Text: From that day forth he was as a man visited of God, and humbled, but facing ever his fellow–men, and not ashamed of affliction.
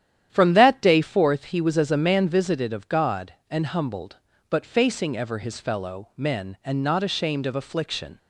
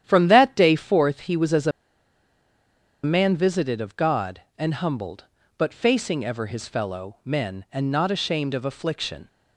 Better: first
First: starts louder than the rest; strong; until 1.3 s; 10.5 dB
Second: starts louder than the rest; strong; until 1.0 s; 10.5 dB // pauses between "a" and "man"; strong; at 1.7 s; 1.3 s long

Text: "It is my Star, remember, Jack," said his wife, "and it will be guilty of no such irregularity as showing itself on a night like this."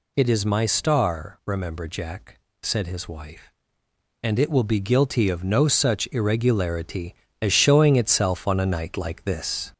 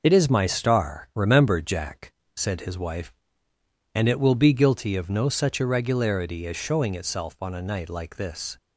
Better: second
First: gets louder; slight; throughout; 3 dB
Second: none

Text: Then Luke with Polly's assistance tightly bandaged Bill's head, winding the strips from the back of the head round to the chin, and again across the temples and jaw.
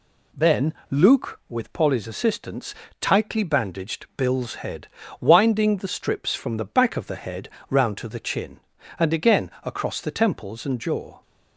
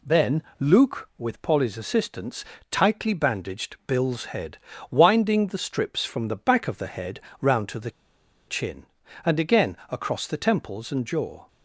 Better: first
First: pauses between "Then" and "Luke"; slight; at 0.7 s; 0.16 s long // pauses between "assistance" and "tightly"; slight; at 2.7 s; 0.26 s long // pauses between "head" and "round"; slight; at 7.4 s; 0.20 s long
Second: pauses between "Then" and "Luke"; slight; at 0.4 s; 0.16 s long // pauses between "assistance" and "tightly"; slight; at 2.4 s; 0.26 s long // pauses between "head" and "round"; slight; at 7.2 s; 0.20 s long // pauses between "the" and "chin"; noticeable; at 7.9 s; 0.57 s long

